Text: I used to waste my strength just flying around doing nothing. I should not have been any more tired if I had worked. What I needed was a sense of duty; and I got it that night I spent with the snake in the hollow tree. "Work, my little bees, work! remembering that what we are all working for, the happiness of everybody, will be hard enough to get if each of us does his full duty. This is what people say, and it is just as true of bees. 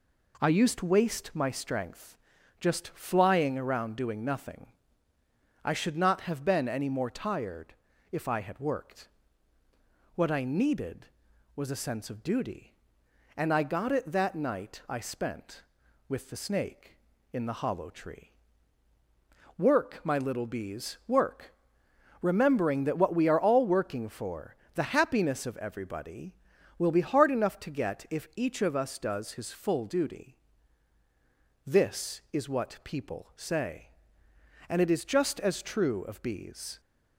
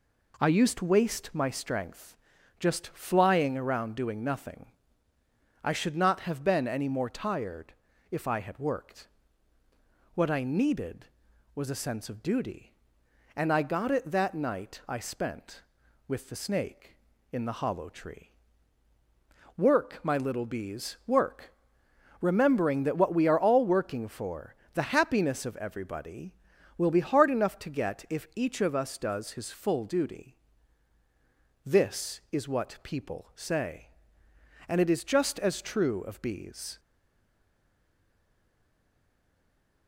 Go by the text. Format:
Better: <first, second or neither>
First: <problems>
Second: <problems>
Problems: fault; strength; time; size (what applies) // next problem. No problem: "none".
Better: first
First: pauses between "strength" and "just"; at 2.1 s; 0.42 s long // pauses between "tired" and "if"; at 7.7 s; 0.38 s long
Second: pauses between "strength" and "just"; at 2.1 s; 0.42 s long // pauses between "tired" and "if"; at 7.7 s; 0.38 s long // stays silent after the last word; strong; from 36.7 s on; 3.1 s long